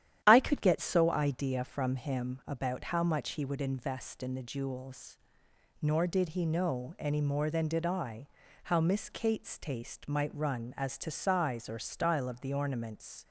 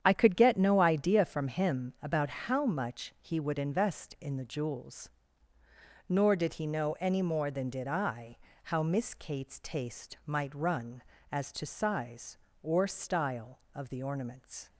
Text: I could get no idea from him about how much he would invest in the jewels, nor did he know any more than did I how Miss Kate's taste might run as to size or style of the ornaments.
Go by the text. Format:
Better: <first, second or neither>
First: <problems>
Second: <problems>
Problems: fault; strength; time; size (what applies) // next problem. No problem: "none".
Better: second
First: starts louder than the rest; strong; until 1.2 s; 11 dB // says "so" for "no"; at 0.7 s // pauses between "I" and "how"; slight; at 8.2 s; 0.36 s long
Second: starts louder than the rest; strong; until 1.0 s; 9 dB // pauses between "I" and "how"; slight; at 8.3 s; 0.28 s long